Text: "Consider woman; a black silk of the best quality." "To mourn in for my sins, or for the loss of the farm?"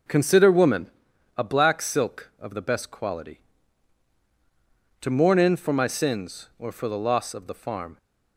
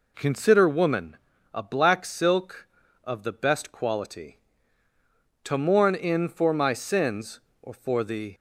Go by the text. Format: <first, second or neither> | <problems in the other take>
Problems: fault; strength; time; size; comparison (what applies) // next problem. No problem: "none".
first | stops before "loss of the farm"; at 8.3 s